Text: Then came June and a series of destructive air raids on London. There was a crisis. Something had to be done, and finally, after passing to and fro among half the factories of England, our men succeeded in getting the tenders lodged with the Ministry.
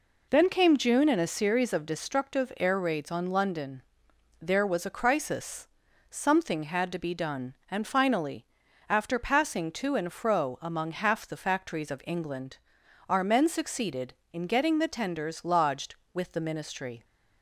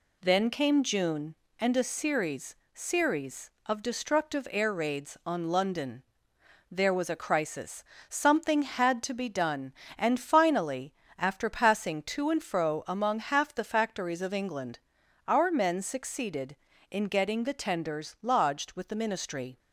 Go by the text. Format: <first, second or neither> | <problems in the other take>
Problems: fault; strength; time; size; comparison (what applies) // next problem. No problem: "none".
first | says "series" twice; at 2.7 s